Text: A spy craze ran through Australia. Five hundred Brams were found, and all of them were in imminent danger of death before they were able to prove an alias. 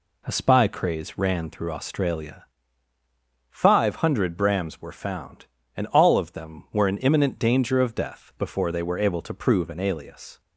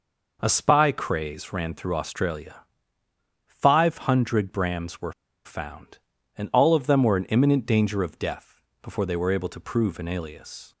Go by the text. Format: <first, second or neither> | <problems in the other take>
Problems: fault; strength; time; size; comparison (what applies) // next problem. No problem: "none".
first | pauses between "were" and "found"; slight; at 5.1 s; 0.32 s long // pauses between "death" and "before"; slight; at 8.6 s; 0.20 s long